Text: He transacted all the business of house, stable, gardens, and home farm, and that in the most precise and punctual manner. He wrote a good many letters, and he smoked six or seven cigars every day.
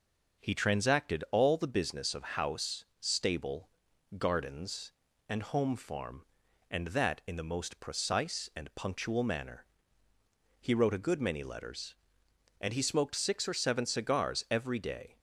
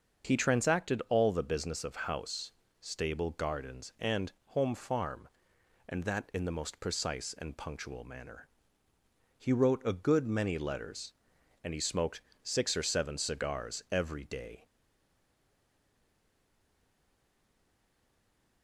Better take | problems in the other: first | starts louder than the rest; until 1.3 s; 6.5 dB // pauses between "smoked" and "six"; slight; at 12.2 s; 0.20 s long // stays silent after the last word; strong; from 14.6 s on; 4.0 s long

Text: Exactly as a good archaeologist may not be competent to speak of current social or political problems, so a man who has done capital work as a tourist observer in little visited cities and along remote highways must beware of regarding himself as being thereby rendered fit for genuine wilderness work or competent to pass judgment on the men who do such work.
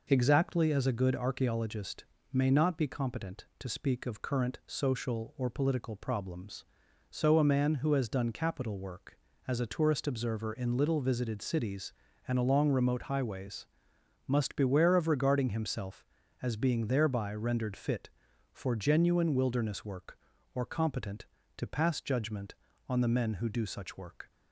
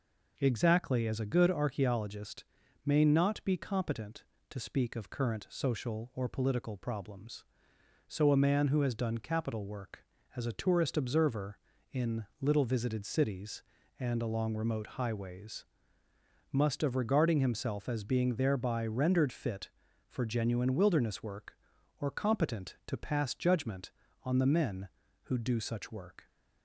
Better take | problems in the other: first | pauses between "archaeologist" and "may"; at 2.4 s; 0.40 s long; slight in the first // pauses between "highways" and "must"; noticeable; at 15.6 s; 0.88 s long; noticeable in the first // skips "beware"; at 16.8 s

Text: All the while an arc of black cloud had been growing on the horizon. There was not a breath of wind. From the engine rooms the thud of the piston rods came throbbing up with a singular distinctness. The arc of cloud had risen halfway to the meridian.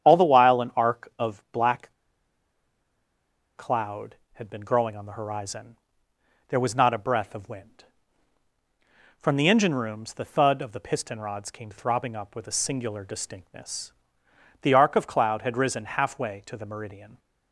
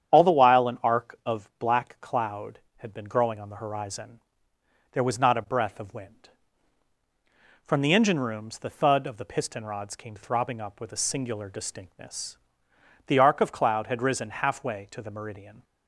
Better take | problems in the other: second | starts louder than the rest; strong; until 1.1 s; 9 dB; strong in the second // pauses between "black" and "cloud"; strong; at 1.9 s; 1.6 s long

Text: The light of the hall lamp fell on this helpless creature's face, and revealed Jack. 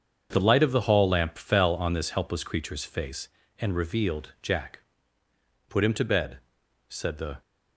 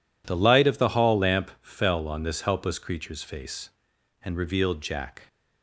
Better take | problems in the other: second | starts louder than the rest; until 1.3 s; 7 dB // goes on to say "Put him to bed said the"; strong; from 5.6 s on; 1.7 s long

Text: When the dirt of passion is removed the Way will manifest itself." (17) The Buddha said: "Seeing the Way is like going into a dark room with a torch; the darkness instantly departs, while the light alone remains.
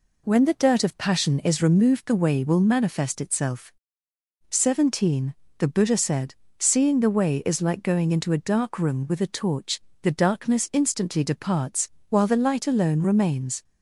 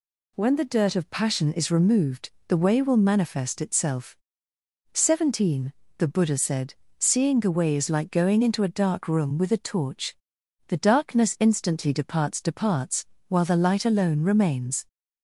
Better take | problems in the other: first | pauses between "removed" and "the"; slight; at 2.3 s; 0.16 s long // says "departs" twice; at 12.4 s

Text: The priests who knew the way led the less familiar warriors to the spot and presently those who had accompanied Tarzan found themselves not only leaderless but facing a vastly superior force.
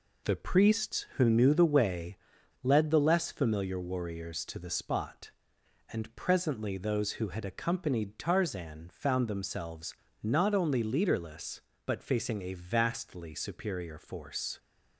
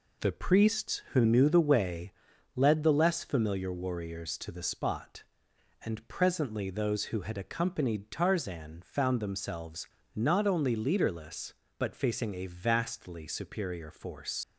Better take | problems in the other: first | pauses between "way" and "led"; noticeable; at 2.1 s; 0.46 s long; noticeable in the first // pauses between "themselves" and "not"; slight; at 9.8 s; 0.30 s long; slight in the first // leaves "force" unfinished; at 14.4 s; 75 ms

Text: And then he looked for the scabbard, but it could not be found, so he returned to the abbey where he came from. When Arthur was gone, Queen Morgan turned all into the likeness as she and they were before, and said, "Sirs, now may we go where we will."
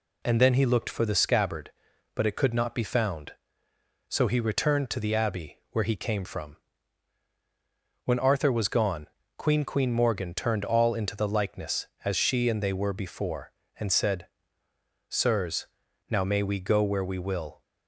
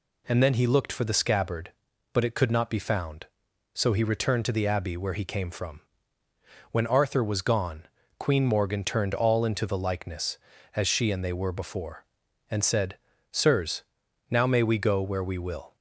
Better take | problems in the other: second | says "Queen" twice; at 9.6 s

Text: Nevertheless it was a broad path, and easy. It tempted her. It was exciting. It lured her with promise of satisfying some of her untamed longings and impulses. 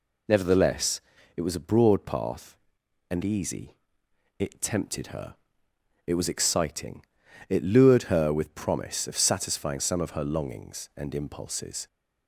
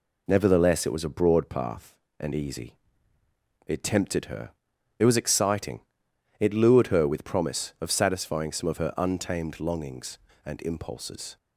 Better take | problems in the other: second | pauses between "Nevertheless" and "it"; slight; at 1.0 s; 0.34 s long // skips "untamed"; at 10.2 s

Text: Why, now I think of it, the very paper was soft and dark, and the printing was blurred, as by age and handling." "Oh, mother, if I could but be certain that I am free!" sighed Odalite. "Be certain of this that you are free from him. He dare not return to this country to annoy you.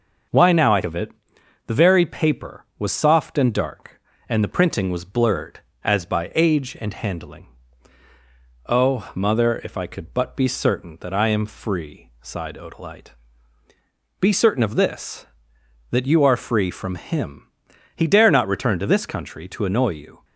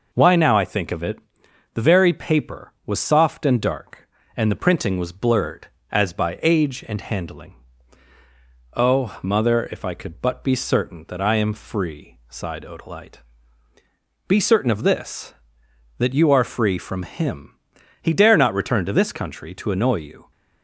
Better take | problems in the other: second | starts louder than the rest; until 1.9 s; 6.5 dB // skips "think"; at 0.8 s

